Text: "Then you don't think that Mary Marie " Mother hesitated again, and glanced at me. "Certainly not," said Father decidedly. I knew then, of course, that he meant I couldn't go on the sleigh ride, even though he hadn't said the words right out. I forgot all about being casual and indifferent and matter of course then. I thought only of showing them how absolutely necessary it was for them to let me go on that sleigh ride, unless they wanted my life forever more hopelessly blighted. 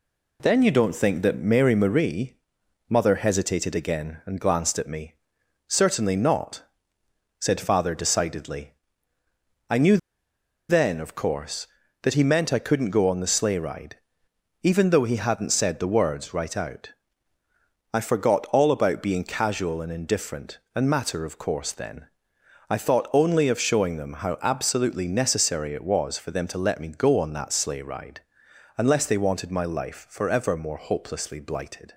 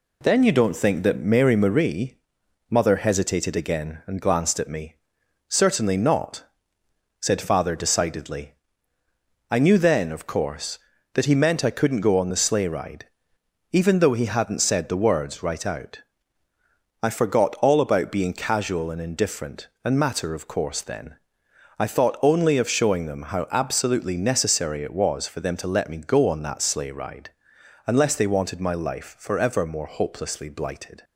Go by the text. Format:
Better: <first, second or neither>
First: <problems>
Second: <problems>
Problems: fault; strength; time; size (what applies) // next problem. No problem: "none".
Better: second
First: pauses between "knew" and "then"; noticeable; at 9.9 s; 0.72 s long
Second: none